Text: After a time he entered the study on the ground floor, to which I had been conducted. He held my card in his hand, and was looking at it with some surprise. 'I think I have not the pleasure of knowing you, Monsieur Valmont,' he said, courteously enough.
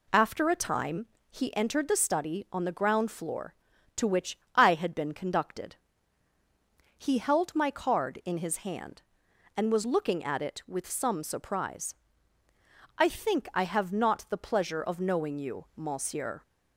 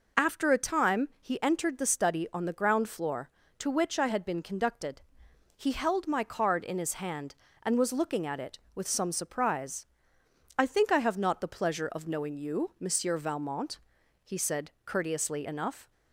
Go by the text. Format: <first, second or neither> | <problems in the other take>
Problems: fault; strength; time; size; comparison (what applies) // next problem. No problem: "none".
second | pauses between "time" and "he"; slight; at 1.0 s; 0.24 s long // pauses between "which" and "I"; slight; at 4.3 s; 0.17 s long // stops before "Valmont he said courteously enough"; at 16.4 s